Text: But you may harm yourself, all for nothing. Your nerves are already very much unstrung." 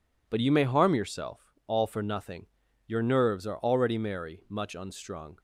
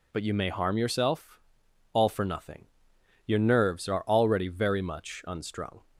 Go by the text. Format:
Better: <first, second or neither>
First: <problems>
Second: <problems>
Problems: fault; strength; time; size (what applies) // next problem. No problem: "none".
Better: second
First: says "merry" for "very"; at 3.9 s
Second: none